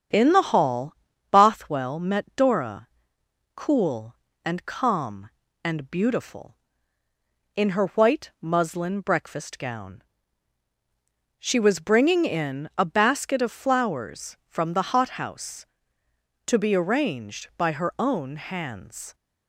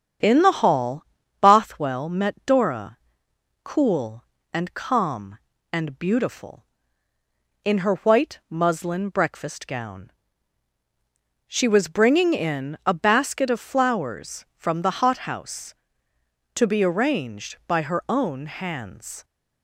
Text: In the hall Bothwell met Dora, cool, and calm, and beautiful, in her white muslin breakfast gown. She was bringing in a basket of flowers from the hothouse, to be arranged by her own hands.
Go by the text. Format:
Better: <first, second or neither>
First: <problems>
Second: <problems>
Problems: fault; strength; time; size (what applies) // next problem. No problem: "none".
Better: neither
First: starts louder than the rest; strong; until 1.5 s; 8 dB // pauses between "hall" and "Bothwell"; at 0.9 s; 0.38 s long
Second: starts louder than the rest; strong; until 1.6 s; 8 dB // pauses between "hall" and "Bothwell"; at 1.0 s; 0.38 s long